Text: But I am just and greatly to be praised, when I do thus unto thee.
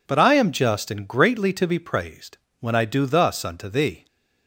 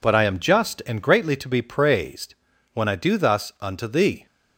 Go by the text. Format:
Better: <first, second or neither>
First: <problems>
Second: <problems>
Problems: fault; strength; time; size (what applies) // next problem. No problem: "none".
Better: neither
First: none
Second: none